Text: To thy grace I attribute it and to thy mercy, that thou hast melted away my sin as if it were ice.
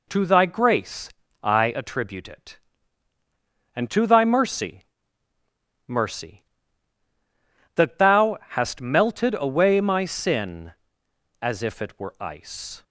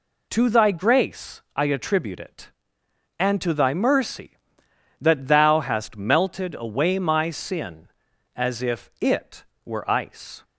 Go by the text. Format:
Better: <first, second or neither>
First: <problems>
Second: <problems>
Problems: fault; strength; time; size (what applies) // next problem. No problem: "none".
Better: second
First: pauses between "grace" and "I"; slight; at 1.1 s; 0.32 s long // says "mercy" twice; at 5.8 s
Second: none